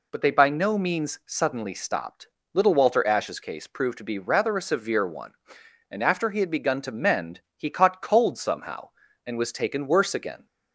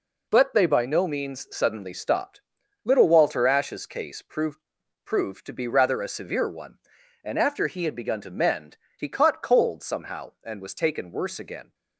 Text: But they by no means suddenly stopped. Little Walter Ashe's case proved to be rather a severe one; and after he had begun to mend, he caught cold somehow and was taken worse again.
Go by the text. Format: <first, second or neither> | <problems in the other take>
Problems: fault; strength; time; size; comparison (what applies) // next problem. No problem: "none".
first | says "proved" twice; at 5.0 s